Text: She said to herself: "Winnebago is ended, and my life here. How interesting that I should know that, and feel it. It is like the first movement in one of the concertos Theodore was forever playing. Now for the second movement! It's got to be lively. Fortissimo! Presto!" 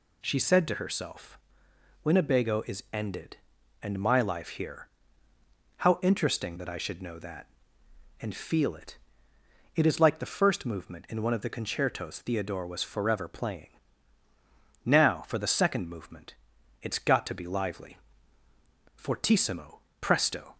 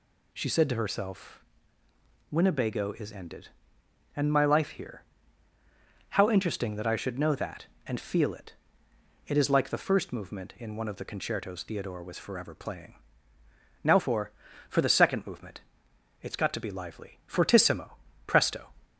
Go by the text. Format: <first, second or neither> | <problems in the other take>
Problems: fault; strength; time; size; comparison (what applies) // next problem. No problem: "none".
first | says "for" twice; at 14.6 s